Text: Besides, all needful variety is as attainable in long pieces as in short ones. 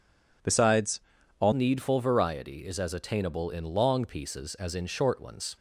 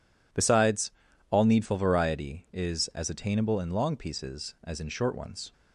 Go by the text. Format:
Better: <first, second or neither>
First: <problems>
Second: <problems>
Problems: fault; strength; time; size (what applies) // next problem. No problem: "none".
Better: second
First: changes voice at "needful"; from 1.5 s on; 4.0 s long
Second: none